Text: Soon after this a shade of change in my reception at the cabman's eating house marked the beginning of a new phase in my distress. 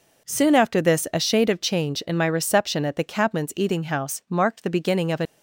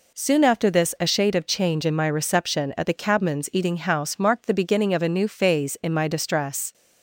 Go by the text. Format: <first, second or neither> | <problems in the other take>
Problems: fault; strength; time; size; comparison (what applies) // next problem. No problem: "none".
second | stops before "new phase in my distress"; at 5.2 s